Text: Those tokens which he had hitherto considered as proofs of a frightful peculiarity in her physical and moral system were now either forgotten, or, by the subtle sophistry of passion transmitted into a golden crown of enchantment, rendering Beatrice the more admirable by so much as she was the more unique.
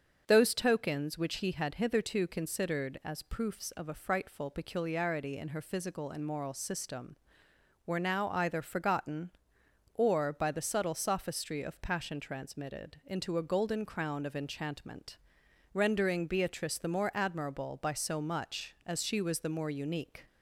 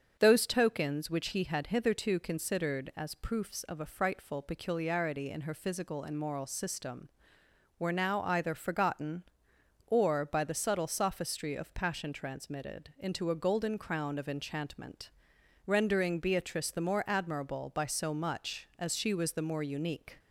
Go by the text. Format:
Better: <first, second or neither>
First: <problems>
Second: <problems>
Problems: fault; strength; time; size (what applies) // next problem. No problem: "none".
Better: neither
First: starts louder than the rest; until 1.2 s; 6.5 dB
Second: starts louder than the rest; until 1.2 s; 6.5 dB